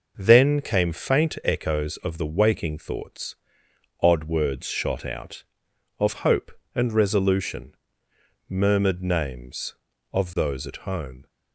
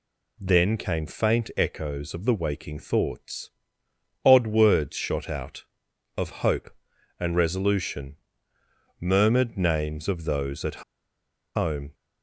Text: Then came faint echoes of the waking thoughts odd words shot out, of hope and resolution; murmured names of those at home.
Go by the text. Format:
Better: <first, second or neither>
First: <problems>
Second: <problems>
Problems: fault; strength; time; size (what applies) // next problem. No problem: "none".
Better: first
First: pauses between "thoughts" and "odd"; noticeable; at 3.3 s; 0.66 s long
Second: pauses between "thoughts" and "odd"; noticeable; at 3.4 s; 0.74 s long // pauses between "at" and "home"; noticeable; at 10.8 s; 0.72 s long